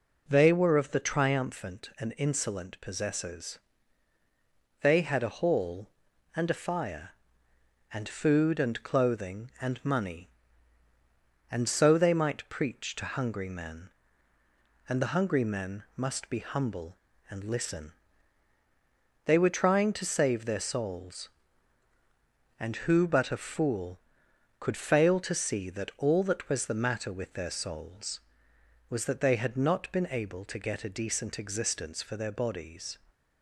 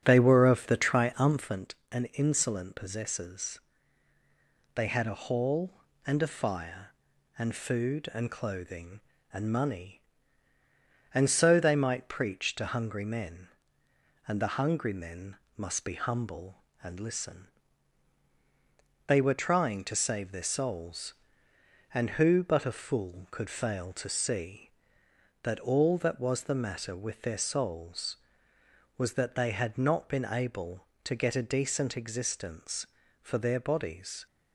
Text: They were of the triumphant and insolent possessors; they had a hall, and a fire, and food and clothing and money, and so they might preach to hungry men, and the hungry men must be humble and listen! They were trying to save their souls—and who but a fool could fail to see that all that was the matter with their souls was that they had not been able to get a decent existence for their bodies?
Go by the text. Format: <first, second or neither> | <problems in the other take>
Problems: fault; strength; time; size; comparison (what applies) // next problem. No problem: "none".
first | starts louder than the rest; strong; until 1.6 s; 8 dB // pauses between "men" and "must"; slight; at 15.3 s; 0.20 s long